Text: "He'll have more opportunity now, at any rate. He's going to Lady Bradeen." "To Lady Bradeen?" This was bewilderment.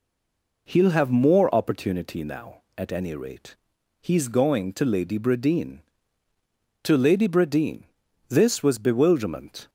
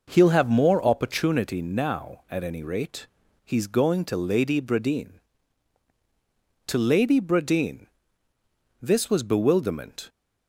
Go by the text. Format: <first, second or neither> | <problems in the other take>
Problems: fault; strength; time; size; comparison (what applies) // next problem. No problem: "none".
second | stays silent before the first word; slight; until 0.6 s; 0.6 s long